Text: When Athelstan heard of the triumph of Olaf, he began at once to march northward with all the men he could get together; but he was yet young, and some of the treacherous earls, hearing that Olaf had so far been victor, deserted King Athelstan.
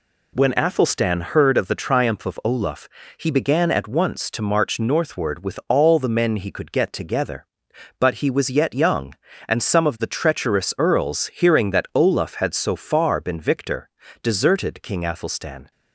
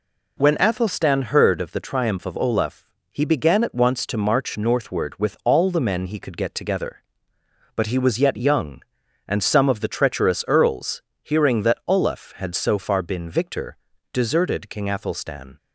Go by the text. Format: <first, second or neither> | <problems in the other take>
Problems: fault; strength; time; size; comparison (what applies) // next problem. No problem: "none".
neither | none